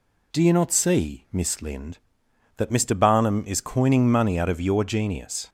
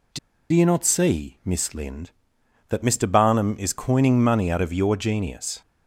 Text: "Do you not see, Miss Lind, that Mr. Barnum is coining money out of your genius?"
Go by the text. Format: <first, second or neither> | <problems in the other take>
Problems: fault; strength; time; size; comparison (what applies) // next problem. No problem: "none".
first | pauses between "Do" and "you"; slight; at 0.1 s; 0.34 s long